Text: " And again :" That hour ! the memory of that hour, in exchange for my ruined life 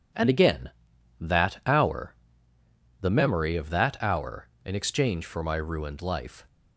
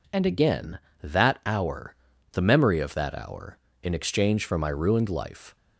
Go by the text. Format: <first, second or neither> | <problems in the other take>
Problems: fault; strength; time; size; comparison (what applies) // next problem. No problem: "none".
neither | none